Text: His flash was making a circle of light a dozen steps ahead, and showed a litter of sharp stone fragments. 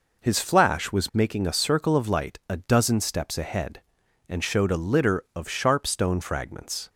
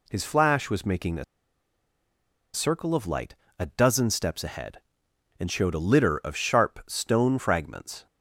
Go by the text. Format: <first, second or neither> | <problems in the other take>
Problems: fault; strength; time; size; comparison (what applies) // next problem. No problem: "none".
first | pauses between "a" and "circle"; strong; at 1.2 s; 1.2 s long // pauses between "light" and "a"; slight; at 3.3 s; 0.24 s long